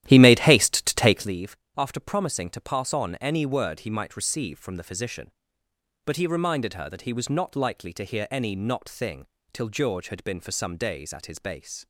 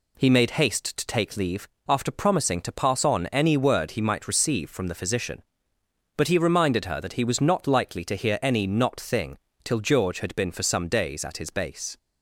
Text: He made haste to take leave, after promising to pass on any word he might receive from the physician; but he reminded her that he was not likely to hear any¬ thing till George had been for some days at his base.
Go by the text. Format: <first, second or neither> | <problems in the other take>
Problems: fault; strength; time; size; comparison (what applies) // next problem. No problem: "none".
second | starts louder than the rest; strong; until 1.3 s; 12.5 dB // pauses between "thing" and "till"; slight; at 9.2 s; 0.28 s long; slight in the second